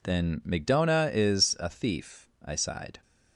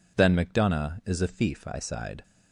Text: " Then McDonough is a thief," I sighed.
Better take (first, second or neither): neither